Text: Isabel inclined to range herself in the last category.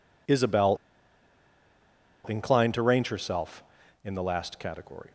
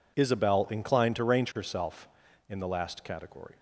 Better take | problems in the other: second | pauses between "Isabel" and "inclined"; strong; at 0.7 s; 1.5 s long

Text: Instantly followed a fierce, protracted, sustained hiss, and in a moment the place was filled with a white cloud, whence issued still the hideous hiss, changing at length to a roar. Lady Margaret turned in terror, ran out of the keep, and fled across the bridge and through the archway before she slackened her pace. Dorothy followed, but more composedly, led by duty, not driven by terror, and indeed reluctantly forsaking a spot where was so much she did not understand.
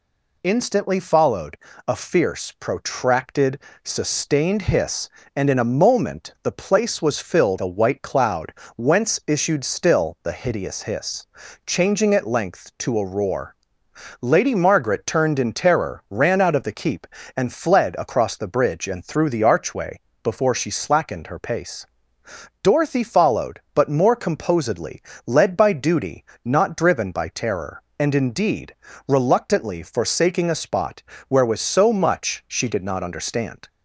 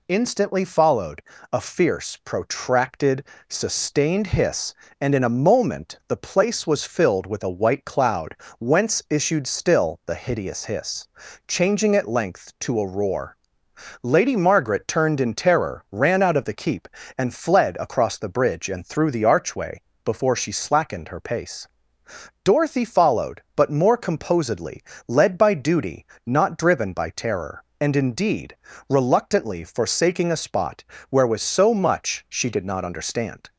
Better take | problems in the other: second | pauses between "followed" and "a"; slight; at 1.5 s; 0.28 s long; slight in the second // skips "with"; at 7.5 s // pauses between "archway" and "before"; slight; at 19.9 s; 0.24 s long; slight in the second // pauses between "indeed" and "reluctantly"; slight; at 28.7 s; 0.34 s long; slight in the second // pauses between "spot" and "where"; slight; at 31.0 s; 0.26 s long; slight in the second

